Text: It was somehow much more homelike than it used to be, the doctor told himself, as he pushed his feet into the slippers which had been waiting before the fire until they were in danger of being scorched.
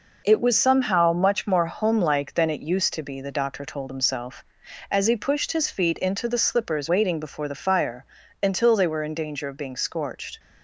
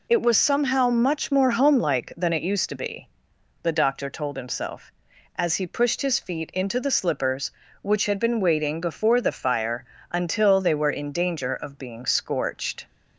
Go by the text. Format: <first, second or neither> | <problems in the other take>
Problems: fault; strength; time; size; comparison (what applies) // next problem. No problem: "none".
second | skips "which had been"; at 6.8 s // pauses between "fire" and "until"; slight; at 8.0 s; 0.36 s long; slight in the second